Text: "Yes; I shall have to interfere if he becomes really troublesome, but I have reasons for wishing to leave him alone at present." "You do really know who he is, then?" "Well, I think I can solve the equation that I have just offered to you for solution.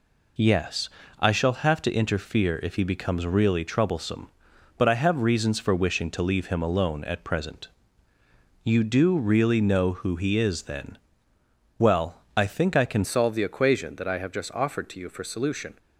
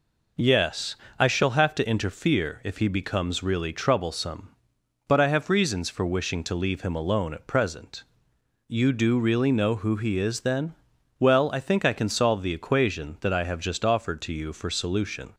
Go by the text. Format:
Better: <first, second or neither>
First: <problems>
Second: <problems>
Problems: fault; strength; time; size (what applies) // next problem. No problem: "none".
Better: second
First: changes voice at "solve"; from 13.0 s on; 2.7 s long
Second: none